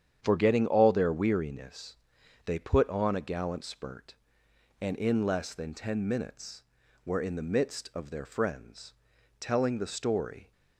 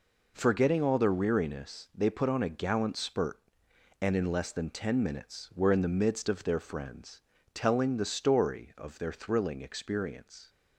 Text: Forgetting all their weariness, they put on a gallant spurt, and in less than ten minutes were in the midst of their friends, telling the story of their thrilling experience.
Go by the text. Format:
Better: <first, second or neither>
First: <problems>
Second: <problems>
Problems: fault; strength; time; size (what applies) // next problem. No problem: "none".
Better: second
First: starts louder than the rest; strong; until 1.2 s; 8.5 dB // stops before "of their thrilling experience"; at 10.5 s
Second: none